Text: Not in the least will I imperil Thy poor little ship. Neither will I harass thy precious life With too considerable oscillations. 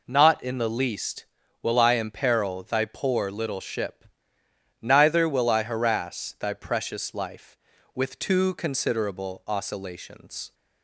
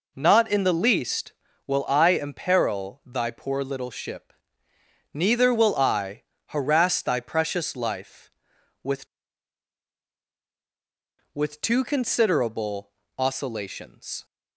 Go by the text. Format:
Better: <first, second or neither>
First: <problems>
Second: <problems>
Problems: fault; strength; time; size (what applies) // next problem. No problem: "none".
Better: first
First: none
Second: pauses between "I" and "harass"; slight; at 6.2 s; 0.24 s long // says "With" twice; at 11.3 s // pauses between "considerable" and "oscillations"; slight; at 12.9 s; 0.26 s long